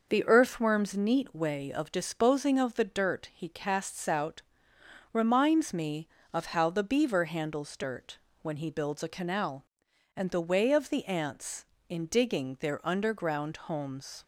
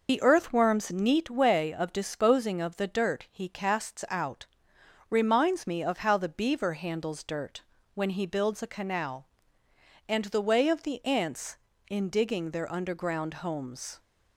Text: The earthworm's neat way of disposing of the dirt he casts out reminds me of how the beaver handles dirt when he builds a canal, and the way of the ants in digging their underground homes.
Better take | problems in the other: first | loses the start of "The"; at 0.0 s; 65 ms // pauses between "out" and "reminds"; noticeable; at 4.4 s; 0.62 s long; noticeable in the first // pauses between "dirt" and "when"; slight; at 7.6 s; 0.32 s long; slight in the first

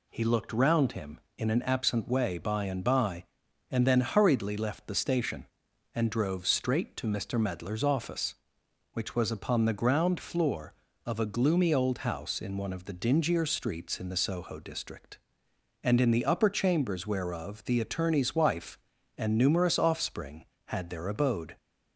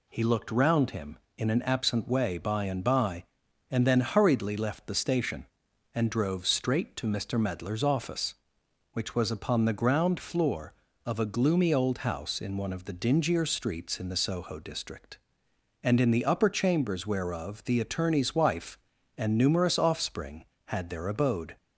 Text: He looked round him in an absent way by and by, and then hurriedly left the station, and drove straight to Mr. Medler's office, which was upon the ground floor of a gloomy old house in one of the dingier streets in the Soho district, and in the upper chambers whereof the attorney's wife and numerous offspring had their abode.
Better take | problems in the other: neither | none

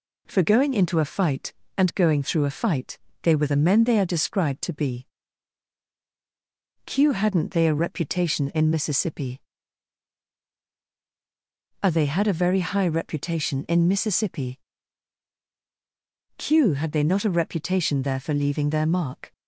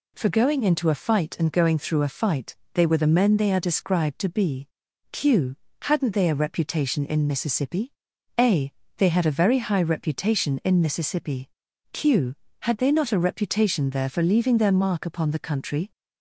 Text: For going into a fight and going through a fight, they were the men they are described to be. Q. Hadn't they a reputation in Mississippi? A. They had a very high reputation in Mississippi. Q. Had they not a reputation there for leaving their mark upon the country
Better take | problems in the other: second | stops before "upon the country"; at 19.3 s

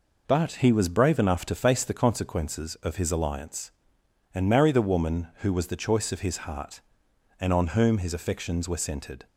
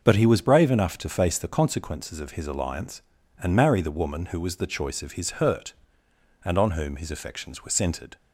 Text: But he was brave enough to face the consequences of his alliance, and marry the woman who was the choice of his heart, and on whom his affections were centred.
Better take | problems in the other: first | starts louder than the rest; until 1.0 s; 6 dB // says "hurt" for "heart"; at 5.3 s

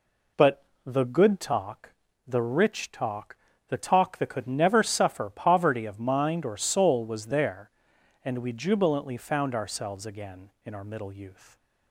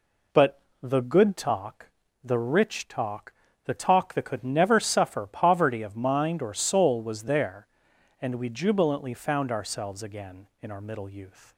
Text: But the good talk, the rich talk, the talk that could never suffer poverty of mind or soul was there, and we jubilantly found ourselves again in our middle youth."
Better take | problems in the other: neither | pauses between "But" and "the"; slight; the same in both

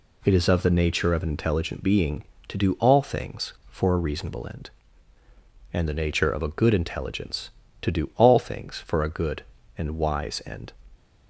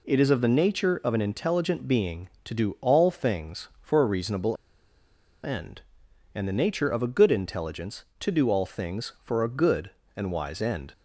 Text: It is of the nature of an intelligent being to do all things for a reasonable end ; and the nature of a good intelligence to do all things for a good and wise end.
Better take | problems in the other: first | pauses between "reasonable" and "end"; noticeable; at 4.5 s; 0.89 s long

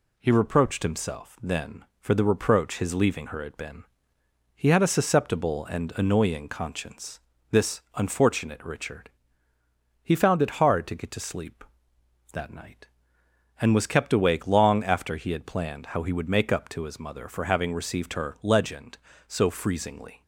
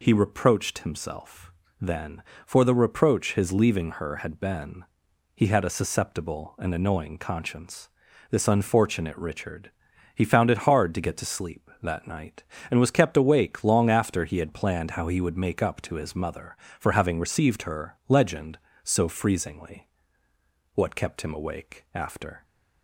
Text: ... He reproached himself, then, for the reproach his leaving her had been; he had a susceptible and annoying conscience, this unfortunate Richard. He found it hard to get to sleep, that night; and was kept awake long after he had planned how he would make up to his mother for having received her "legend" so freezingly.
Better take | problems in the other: first | goes on to say "What kept him awake after"; strong; from 20.7 s on; 1.7 s long

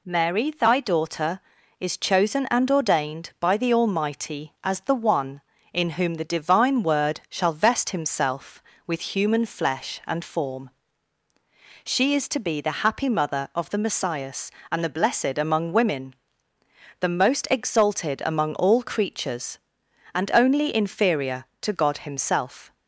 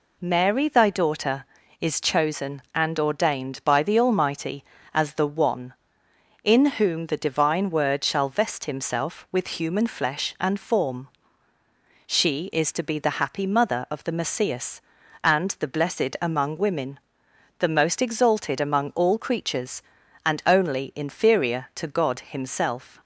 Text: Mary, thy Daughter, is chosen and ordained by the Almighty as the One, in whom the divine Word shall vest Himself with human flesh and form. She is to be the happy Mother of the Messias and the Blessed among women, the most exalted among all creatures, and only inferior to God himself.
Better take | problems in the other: neither | none

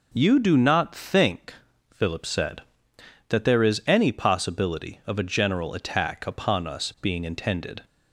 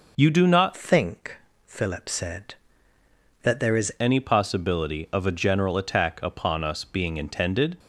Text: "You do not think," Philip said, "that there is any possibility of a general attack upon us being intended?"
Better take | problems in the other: first | changes voice from "think" to "is"; from 0.7 to 3.9 s; 3.2 s long

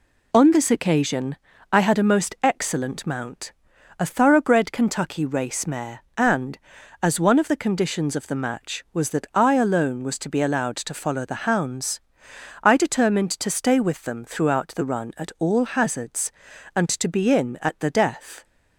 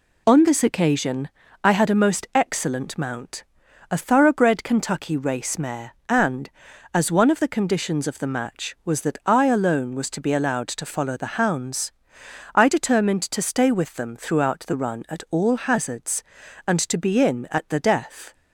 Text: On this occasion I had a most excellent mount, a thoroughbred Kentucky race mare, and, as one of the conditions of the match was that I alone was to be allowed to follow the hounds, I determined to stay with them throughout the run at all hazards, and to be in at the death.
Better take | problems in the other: neither | pauses between "occasion" and "I"; slight; the same in both

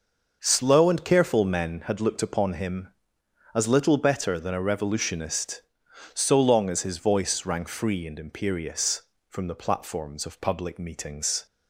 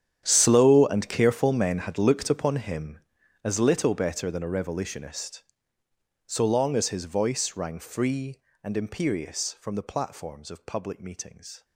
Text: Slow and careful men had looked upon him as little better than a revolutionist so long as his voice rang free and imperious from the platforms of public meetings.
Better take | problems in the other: first | gets quieter; strong; throughout; 18 dB

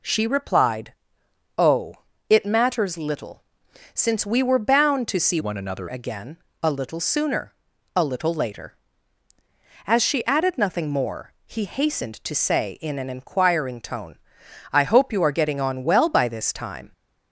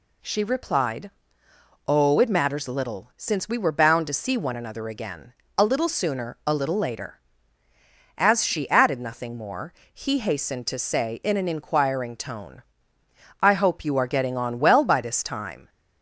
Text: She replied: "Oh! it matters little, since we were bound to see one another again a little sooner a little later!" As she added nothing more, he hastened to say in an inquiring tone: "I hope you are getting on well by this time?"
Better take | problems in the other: second | changes voice from "one" to "another"; from 5.3 to 5.8 s; 0.5 s long // pauses between "again" and "a"; slight; at 6.3 s; 0.24 s long; slight in the second // pauses between "sooner" and "a"; at 7.5 s; 0.42 s long

